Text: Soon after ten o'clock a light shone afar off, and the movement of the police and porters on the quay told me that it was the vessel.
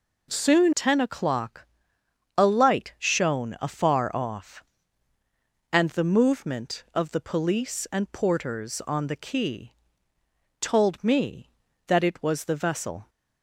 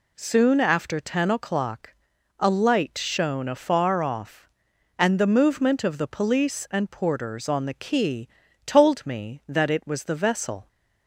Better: second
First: skips "after"; at 0.7 s // pauses between "o'clock" and "a"; noticeable; at 1.6 s; 0.72 s long // pauses between "quay" and "told"; noticeable; at 9.7 s; 0.88 s long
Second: pauses between "o'clock" and "a"; at 1.9 s; 0.44 s long // pauses between "quay" and "told"; slight; at 8.2 s; 0.36 s long

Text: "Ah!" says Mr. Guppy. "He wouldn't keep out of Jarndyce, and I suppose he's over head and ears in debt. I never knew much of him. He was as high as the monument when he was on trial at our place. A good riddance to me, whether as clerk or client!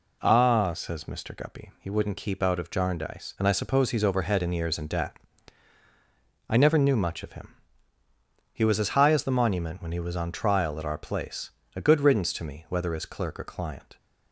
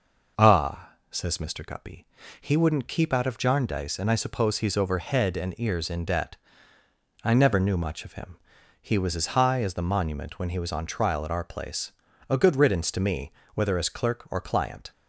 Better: neither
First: none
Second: none

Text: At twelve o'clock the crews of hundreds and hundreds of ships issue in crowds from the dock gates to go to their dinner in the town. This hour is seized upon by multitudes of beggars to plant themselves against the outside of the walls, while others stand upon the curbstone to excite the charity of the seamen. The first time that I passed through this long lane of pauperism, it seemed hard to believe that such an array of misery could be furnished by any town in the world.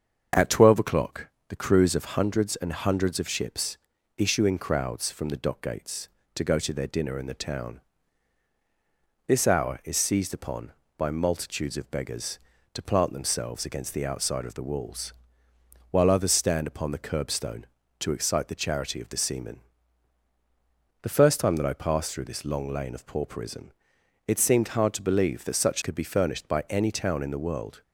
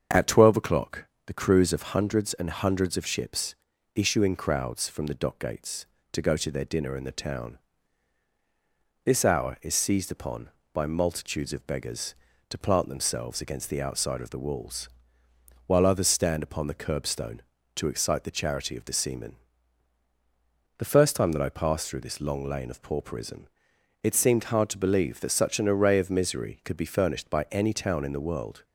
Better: second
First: starts louder than the rest; until 1.5 s; 7 dB // pauses between "o'clock" and "the"; slight; at 1.2 s; 0.20 s long // pauses between "ships" and "issue"; at 3.7 s; 0.40 s long // skips "an array of misery"; at 25.8 s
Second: starts louder than the rest; until 1.3 s; 7 dB // pauses between "o'clock" and "the"; slight; at 1.0 s; 0.20 s long // pauses between "ships" and "issue"; at 3.5 s; 0.40 s long

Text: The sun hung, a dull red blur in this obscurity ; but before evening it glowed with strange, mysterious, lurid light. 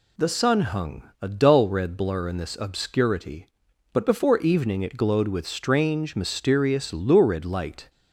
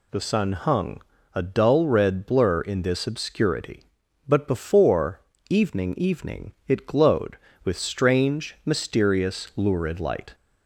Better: first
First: none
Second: pauses between "before" and "evening"; slight; at 5.2 s; 0.28 s long // says "evening" twice; at 5.9 s

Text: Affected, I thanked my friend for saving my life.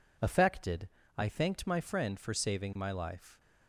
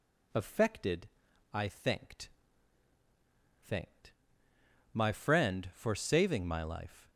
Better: first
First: none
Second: says "thanked" twice; at 3.6 s

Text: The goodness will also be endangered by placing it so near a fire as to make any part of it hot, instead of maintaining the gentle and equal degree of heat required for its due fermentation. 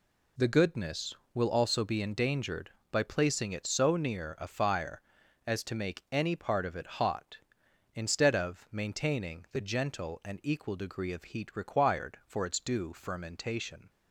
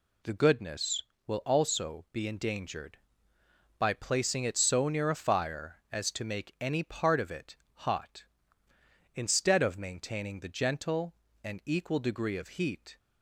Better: first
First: none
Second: pauses between "it" and "hot"; slight; at 7.5 s; 0.18 s long // stops before "required for its due fermentation"; at 12.9 s

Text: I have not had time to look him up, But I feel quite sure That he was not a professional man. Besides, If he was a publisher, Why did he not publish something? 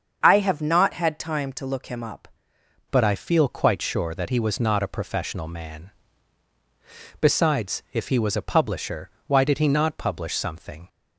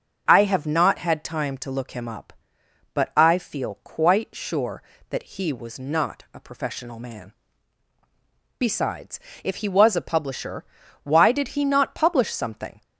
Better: second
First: starts louder than the rest; until 1.2 s; 7 dB // changes voice at "But"; from 2.9 s on; 7.9 s long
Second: starts louder than the rest; until 1.2 s; 6.5 dB

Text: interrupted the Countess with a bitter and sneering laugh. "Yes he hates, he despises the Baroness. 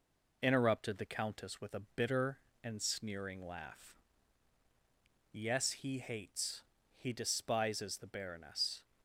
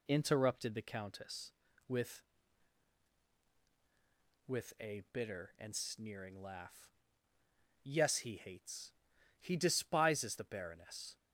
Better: first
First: none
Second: says "with" twice; at 4.4 s

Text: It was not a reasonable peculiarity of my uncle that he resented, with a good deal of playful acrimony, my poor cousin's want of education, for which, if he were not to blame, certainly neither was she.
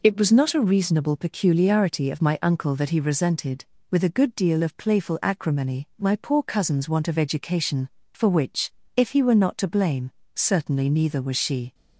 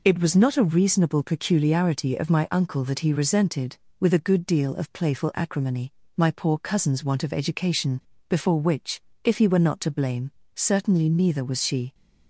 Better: first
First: none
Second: says "before" for "for"; at 8.2 s

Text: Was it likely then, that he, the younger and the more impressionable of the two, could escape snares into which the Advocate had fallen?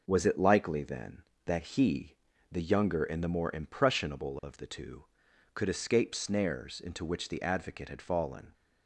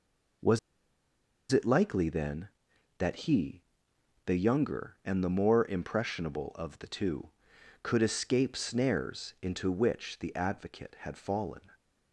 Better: first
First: none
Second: pauses between "Was" and "it"; noticeable; at 0.5 s; 0.92 s long

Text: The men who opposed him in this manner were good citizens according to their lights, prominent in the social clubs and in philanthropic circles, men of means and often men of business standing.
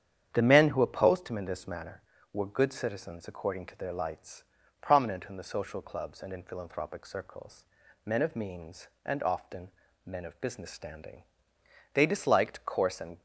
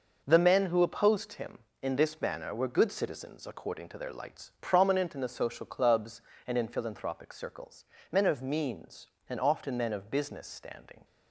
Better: second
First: starts louder than the rest; strong; until 1.3 s; 9 dB // pauses between "often" and "men"; slight; at 9.7 s; 0.34 s long // goes on to say "They disliked coarse and"; noticeable; from 11.9 s on; 1.2 s long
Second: none

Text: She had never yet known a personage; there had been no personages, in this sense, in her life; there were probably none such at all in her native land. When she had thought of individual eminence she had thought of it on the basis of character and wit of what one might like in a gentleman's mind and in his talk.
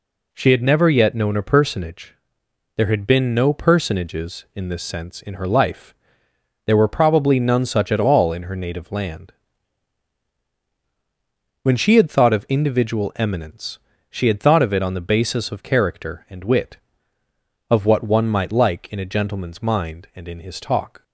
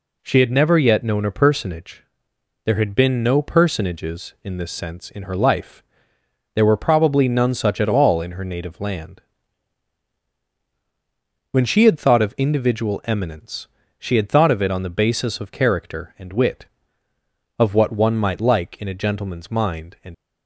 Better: first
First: pauses between "eminence" and "she"; slight; at 13.7 s; 0.30 s long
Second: pauses between "eminence" and "she"; slight; at 13.6 s; 0.30 s long // stops before "in his talk"; at 20.1 s

